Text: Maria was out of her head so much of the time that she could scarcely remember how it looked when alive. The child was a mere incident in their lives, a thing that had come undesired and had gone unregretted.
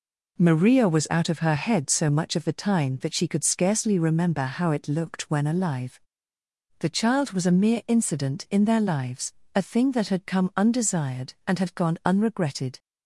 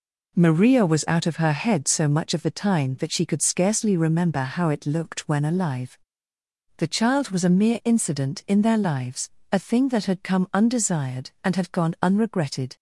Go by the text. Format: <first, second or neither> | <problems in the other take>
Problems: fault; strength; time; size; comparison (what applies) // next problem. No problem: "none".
neither | none